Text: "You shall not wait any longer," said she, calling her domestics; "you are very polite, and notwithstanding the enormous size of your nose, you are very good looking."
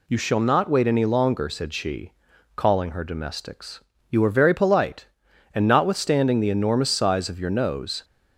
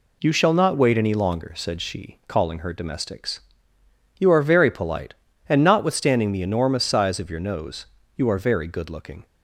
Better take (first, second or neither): second